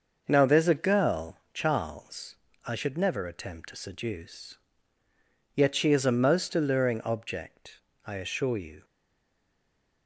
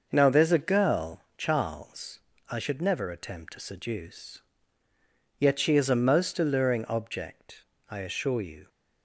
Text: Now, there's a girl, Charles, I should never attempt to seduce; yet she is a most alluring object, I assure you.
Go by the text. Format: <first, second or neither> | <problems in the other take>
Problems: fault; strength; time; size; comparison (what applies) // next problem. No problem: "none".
second | starts louder than the rest; noticeable; until 1.2 s; 6 dB; noticeable in the second // stays silent after the last word; noticeable; from 8.8 s on; 1.2 s long